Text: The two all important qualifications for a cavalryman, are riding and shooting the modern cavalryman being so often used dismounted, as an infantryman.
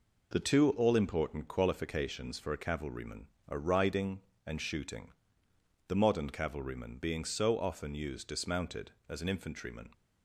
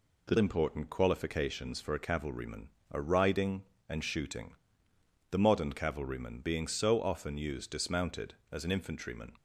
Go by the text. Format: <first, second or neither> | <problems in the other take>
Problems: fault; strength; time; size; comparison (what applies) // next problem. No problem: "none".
first | skips "two all"; at 0.3 s // pauses between "shooting" and "the"; noticeable; at 4.5 s; 0.78 s long; noticeable in the first